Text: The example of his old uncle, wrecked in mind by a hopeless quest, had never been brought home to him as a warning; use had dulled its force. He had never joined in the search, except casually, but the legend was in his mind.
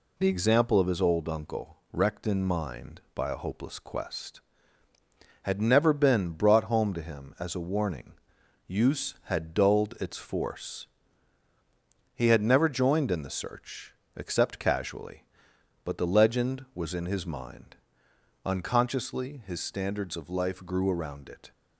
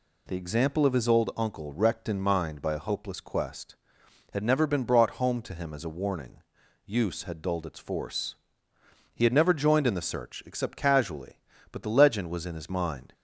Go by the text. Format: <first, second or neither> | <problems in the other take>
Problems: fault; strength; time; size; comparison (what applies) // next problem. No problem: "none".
second | goes on to say "Unconsciously his standards of life grew around it"; strong; from 18.4 s on; 3.0 s long